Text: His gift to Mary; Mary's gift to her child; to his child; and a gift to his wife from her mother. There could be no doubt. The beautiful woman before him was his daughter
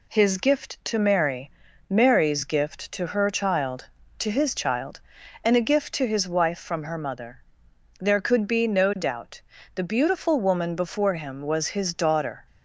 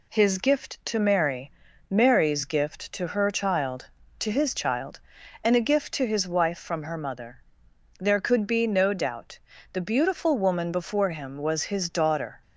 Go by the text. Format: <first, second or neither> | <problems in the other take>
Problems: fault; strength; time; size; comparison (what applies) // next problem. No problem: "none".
neither | none